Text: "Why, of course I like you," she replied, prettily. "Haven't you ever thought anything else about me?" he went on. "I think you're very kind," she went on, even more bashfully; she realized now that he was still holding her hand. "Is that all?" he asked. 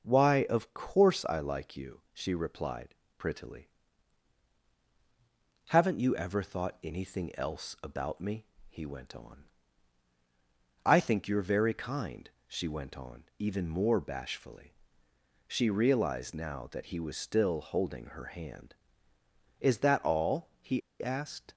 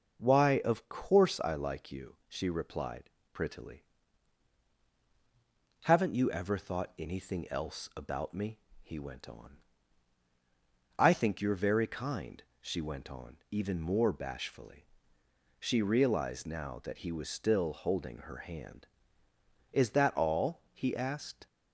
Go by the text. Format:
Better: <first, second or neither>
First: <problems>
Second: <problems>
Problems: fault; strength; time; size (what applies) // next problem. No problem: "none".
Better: second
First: pauses between "he" and "asked"; slight; at 20.8 s; 0.21 s long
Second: none